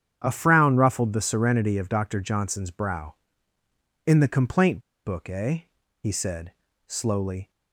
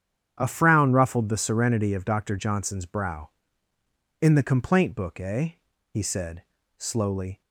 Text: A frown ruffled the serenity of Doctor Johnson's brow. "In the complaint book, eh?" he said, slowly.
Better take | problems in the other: second | starts louder than the rest; strong; until 1.2 s; 8.5 dB; strong in the second // pauses between "complaint" and "book"; slight; at 4.8 s; 0.24 s long

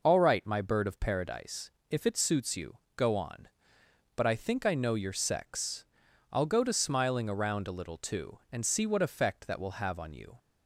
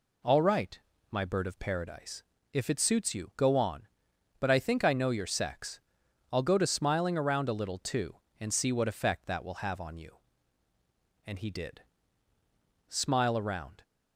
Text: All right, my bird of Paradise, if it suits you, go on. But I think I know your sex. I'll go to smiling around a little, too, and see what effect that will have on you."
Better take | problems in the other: first | goes on to say "And he did smile around"; strong; from 11.2 s on; 2.5 s long

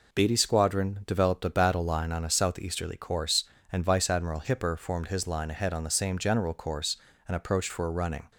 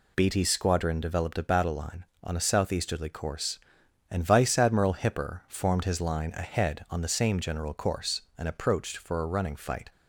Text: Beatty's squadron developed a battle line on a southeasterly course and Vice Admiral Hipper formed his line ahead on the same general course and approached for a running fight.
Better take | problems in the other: second | stops before "fight"; at 8.3 s

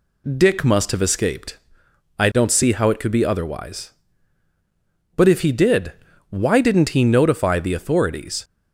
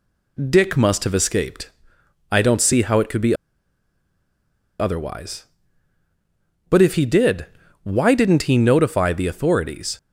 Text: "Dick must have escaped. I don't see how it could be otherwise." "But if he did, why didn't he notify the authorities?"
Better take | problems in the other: first | pauses between "be" and "otherwise"; strong; at 3.3 s; 1.4 s long

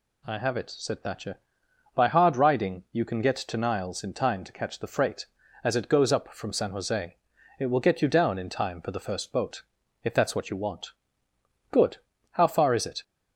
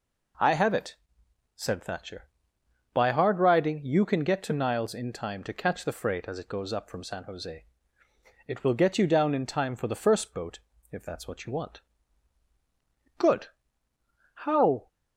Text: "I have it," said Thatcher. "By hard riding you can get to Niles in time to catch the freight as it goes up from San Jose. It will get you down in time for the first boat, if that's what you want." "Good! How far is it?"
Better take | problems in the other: first | stops before "far is it"; at 14.8 s

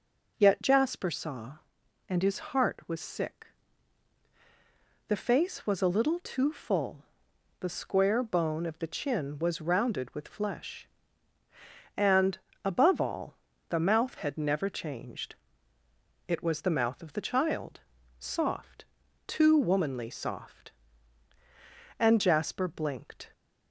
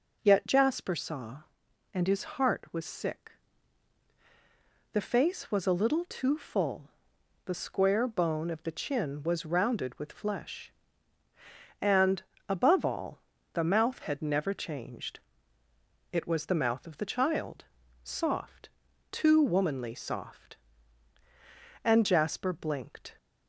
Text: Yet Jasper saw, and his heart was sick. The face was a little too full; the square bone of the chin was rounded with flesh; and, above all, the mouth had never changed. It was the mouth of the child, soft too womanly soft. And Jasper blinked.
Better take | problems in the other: neither | pauses between "soft" and "too"; the same in both

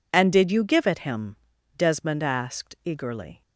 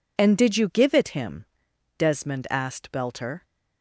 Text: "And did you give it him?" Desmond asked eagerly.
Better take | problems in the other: first | says "belter" for "eagerly"; at 2.9 s

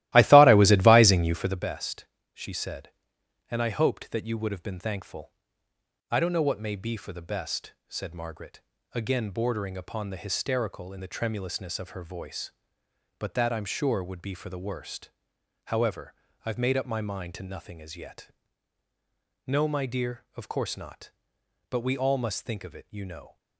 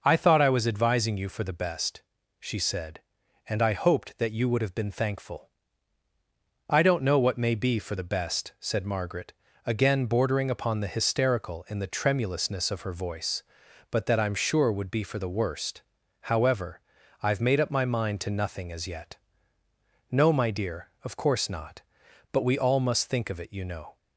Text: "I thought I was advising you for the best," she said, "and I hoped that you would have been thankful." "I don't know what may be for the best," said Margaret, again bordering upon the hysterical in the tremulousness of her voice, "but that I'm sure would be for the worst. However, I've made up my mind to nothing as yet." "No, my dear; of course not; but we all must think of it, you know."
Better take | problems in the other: second | starts louder than the rest; strong; until 1.6 s; 16 dB

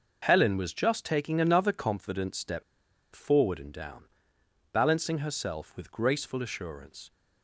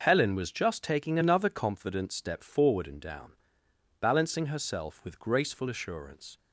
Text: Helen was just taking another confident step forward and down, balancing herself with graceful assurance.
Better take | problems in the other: second | pauses between "step" and "forward"; noticeable; at 2.6 s; 0.51 s long

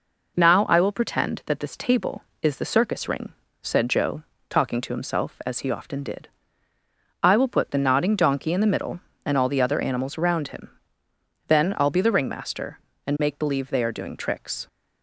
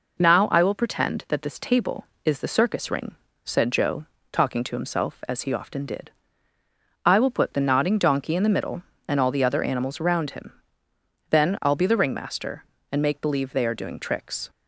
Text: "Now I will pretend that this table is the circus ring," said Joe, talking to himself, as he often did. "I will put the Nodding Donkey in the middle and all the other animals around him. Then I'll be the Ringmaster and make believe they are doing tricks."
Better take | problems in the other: neither | none

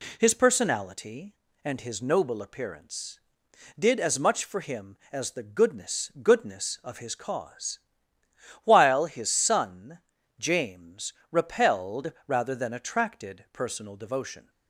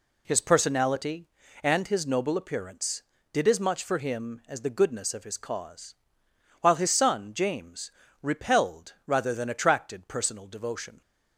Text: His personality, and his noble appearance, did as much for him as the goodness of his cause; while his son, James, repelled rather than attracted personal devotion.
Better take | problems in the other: second | says "goodness" twice; at 6.2 s

